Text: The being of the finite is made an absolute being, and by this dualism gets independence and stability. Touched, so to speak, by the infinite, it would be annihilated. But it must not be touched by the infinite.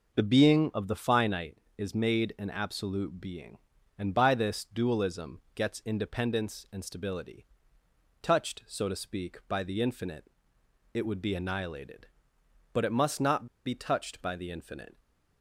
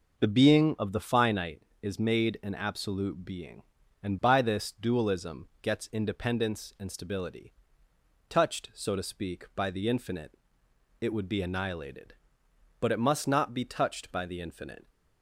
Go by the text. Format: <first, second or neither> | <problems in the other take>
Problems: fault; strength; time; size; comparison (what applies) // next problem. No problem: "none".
second | pauses between "not" and "be"; slight; at 13.4 s; 0.19 s long